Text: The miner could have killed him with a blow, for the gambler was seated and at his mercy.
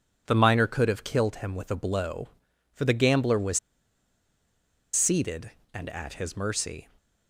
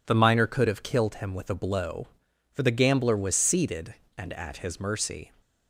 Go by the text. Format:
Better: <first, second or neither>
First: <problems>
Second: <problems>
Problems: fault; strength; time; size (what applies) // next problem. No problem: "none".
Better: second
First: pauses between "was" and "seated"; strong; at 3.5 s; 1.3 s long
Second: none